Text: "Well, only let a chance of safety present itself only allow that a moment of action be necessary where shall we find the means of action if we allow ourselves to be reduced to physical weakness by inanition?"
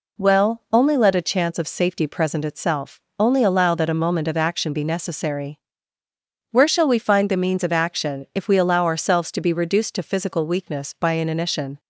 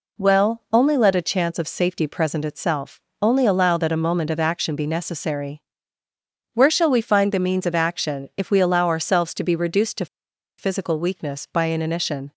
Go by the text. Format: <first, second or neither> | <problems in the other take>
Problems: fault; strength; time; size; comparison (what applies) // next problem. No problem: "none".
first | pauses between "itself" and "only"; slight; at 3.0 s; 0.22 s long; slight in the first // pauses between "necessary" and "where"; noticeable; at 5.6 s; 0.92 s long; noticeable in the first // pauses between "to" and "physical"; noticeable; at 10.0 s; 0.54 s long